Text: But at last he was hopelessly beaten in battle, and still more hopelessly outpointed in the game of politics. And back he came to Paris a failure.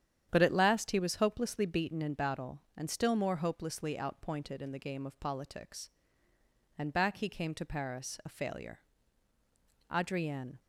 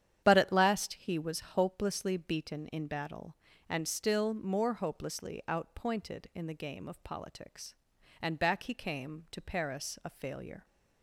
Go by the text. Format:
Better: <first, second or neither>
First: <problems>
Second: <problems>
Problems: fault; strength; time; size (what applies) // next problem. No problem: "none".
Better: second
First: starts louder than the rest; strong; until 1.3 s; 9 dB // goes on to say "Adrienne"; noticeable; from 9.9 s on; 0.68 s long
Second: starts louder than the rest; strong; until 1.2 s; 9.5 dB